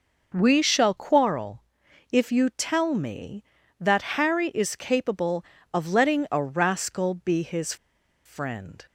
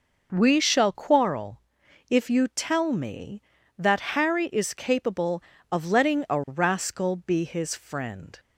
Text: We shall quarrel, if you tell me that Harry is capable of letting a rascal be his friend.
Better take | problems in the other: second | pauses between "his" and "friend"; noticeable; at 7.7 s; 0.50 s long

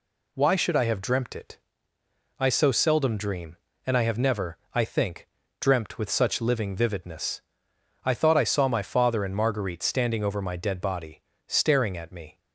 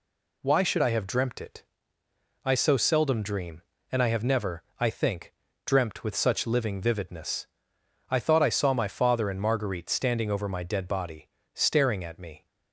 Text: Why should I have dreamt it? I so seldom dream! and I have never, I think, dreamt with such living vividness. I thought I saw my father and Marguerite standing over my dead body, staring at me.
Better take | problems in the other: neither | none

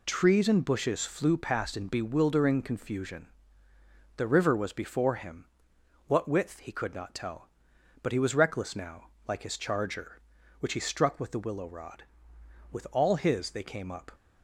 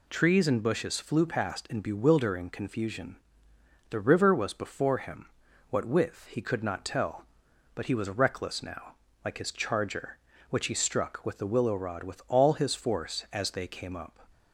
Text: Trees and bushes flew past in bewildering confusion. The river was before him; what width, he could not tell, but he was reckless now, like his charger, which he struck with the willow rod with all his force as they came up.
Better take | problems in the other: second | skips "force as"; at 13.5 s

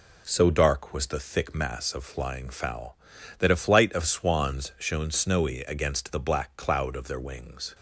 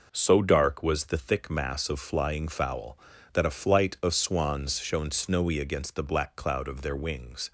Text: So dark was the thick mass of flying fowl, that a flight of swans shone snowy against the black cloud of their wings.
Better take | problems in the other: first | gets quieter; throughout; 6.5 dB

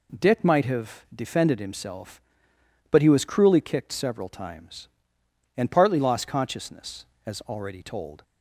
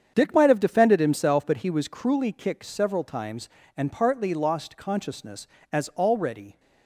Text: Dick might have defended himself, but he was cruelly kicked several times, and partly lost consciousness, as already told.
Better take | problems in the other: first | starts louder than the rest; strong; until 1.1 s; 8 dB // stops before "told"; at 6.5 s

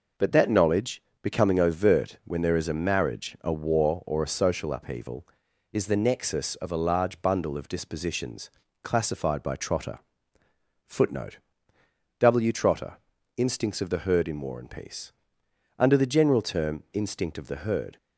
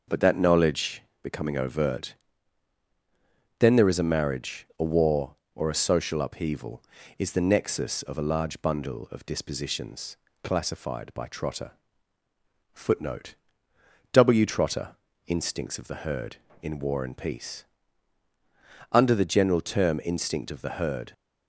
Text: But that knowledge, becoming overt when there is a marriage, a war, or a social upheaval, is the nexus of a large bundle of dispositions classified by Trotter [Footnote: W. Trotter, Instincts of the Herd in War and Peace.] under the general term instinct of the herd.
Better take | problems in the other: first | says "then" for "when"; at 3.5 s // pauses between "dispositions" and "classified"; slight; at 10.1 s; 0.30 s long; slight in the first // pauses between "Trotter" and "Footnote"; at 11.7 s; 1.0 s long; noticeable in the first

